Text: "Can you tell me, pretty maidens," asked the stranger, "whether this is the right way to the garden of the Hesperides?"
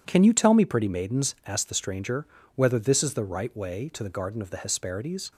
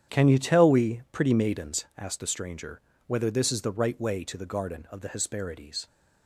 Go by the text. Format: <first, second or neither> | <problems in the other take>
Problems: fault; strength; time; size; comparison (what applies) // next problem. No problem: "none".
first | starts louder than the rest; strong; until 1.2 s; 9.5 dB // says "we" for "me"; at 0.6 s